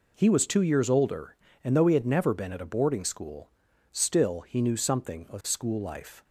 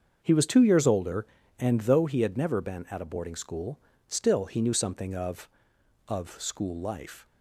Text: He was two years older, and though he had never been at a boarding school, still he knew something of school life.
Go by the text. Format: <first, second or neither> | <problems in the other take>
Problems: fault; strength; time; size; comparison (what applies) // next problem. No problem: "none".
first | starts louder than the rest; until 1.2 s; 6.5 dB // says "of" twice; at 6.0 s